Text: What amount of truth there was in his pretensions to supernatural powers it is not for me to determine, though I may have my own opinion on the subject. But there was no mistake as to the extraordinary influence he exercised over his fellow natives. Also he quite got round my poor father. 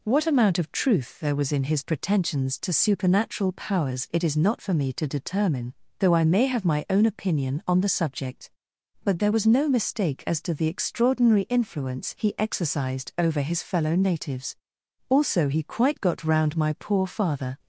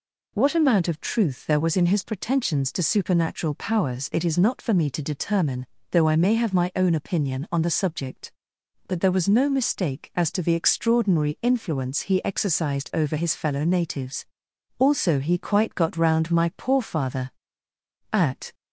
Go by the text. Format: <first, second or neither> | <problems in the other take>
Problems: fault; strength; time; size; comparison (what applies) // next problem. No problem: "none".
first | goes on to say "At"; slight; from 18.0 s on; 0.44 s long